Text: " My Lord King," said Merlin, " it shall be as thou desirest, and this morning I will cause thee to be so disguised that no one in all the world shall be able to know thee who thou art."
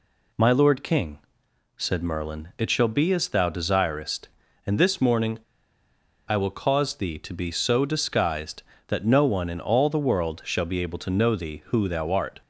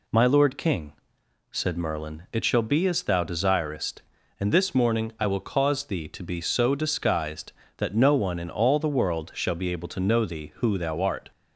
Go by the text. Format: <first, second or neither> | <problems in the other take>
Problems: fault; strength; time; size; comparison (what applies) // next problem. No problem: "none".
second | pauses between "morning" and "I"; noticeable; at 5.3 s; 0.88 s long